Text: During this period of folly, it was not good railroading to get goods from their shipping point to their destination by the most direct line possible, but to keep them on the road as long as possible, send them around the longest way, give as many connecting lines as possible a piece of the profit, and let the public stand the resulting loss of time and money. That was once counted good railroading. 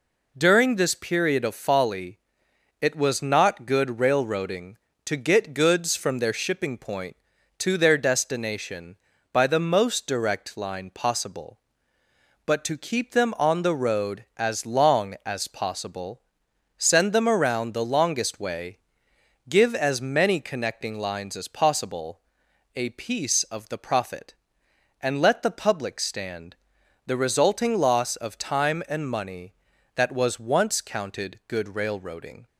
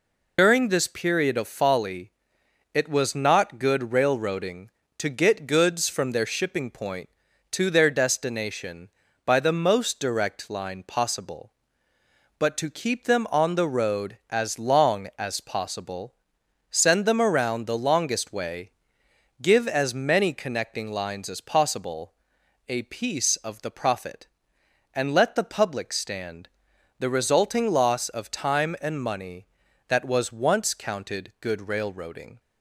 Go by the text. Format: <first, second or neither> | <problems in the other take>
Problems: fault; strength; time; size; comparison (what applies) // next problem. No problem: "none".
first | loses the start of "During"; at 0.3 s; 100 ms // pauses between "possible" and "a"; noticeable; at 22.1 s; 0.56 s long; noticeable in the first // pauses between "stand" and "the"; noticeable; at 26.4 s; 0.50 s long; noticeable in the first